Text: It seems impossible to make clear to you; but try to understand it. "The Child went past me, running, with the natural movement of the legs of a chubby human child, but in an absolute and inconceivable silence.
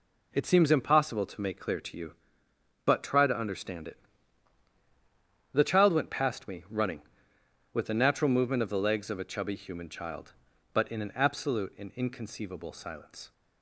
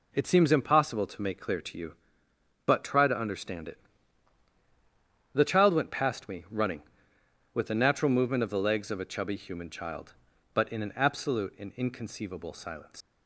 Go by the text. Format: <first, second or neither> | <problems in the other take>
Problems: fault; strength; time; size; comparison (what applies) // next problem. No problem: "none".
first | leaves "silence" unfinished; at 13.0 s; 130 ms